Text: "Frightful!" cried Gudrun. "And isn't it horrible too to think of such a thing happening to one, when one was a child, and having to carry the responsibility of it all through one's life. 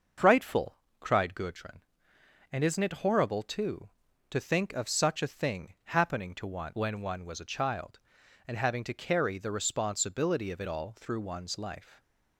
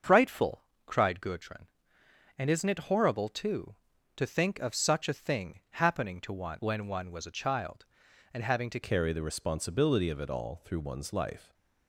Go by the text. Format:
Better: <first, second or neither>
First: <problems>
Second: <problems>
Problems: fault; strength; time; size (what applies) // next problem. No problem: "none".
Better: first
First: starts louder than the rest; until 1.4 s; 6 dB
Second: starts louder than the rest; until 1.2 s; 6.5 dB // changes voice at "carry"; from 8.8 s on; 2.7 s long